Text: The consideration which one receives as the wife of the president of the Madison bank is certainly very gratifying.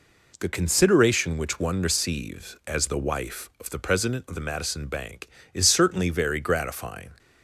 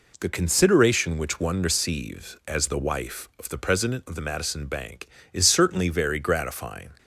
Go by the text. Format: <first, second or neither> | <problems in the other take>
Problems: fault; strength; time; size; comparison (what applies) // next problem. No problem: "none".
neither | none